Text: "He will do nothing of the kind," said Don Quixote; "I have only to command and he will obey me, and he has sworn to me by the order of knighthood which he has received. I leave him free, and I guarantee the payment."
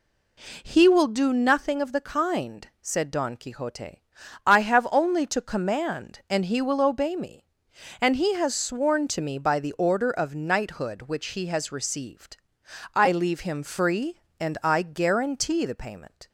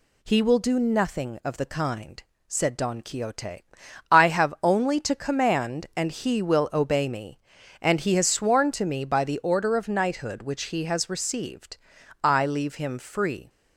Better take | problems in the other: first | stops before "and I guarantee the payment"; at 13.4 s

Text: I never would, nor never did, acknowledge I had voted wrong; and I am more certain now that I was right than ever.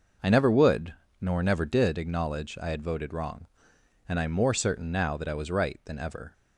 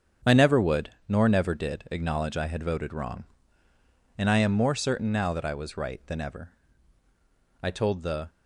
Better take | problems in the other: first | starts louder than the rest; strong; until 1.4 s; 7.5 dB // goes on to say "I told the"; noticeable; from 7.6 s on; 0.68 s long

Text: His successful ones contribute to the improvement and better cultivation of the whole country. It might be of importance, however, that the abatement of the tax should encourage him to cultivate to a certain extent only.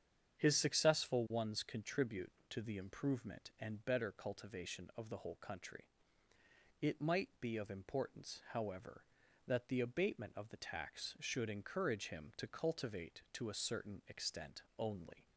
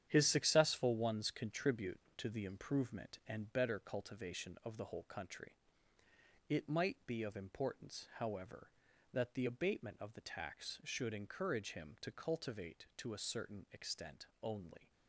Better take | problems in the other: first | gets quieter; strong; throughout; 8 dB // starts louder than the rest; strong; until 1.1 s; 9.5 dB; strong in the first // pauses between "extent" and "only"; slight; at 14.2 s; 0.18 s long; slight in the first

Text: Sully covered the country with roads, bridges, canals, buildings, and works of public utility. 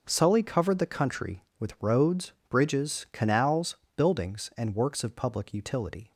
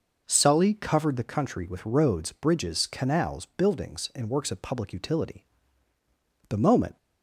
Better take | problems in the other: first | goes on to say "The moment"; slight; from 6.4 s on; 0.48 s long

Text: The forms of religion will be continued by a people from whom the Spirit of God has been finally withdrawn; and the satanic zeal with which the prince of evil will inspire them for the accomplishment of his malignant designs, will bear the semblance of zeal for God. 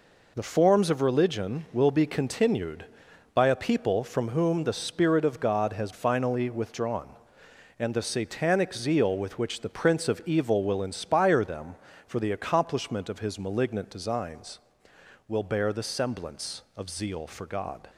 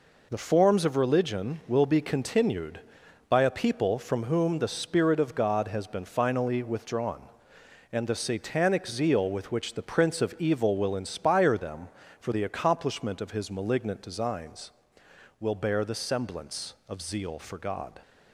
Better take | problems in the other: second | skips "been"; at 5.9 s

